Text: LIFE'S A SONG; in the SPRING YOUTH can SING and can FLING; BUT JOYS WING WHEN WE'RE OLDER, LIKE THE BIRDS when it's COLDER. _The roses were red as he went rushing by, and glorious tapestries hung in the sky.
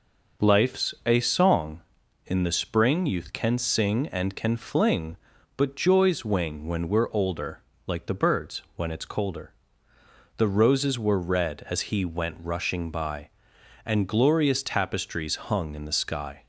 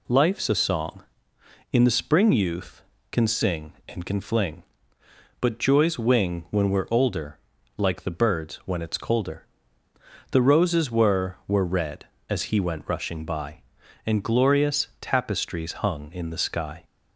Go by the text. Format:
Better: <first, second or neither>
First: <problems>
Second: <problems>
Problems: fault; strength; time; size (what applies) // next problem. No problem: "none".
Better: first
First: none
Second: says "were" twice; at 11.4 s // pauses between "glorious" and "tapestries"; slight; at 14.8 s; 0.16 s long